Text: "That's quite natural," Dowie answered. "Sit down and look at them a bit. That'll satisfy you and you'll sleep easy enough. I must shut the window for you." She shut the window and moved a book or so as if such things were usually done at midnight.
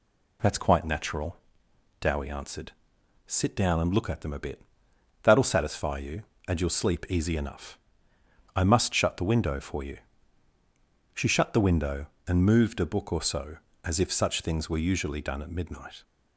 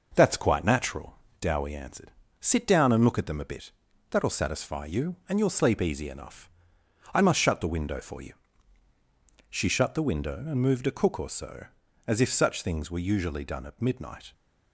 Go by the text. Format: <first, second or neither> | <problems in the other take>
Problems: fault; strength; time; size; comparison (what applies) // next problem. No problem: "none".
first | says "cook" for "book"; at 10.9 s